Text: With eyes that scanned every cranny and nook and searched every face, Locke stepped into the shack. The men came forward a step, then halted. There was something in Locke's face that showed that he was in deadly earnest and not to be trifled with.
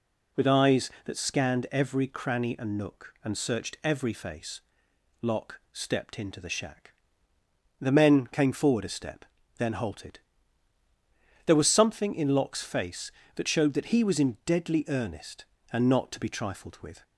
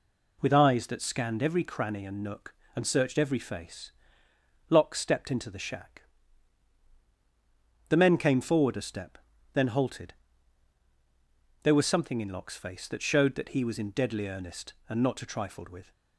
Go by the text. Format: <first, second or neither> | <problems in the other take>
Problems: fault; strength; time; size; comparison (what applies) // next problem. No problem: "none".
first | skips "be"; at 15.2 s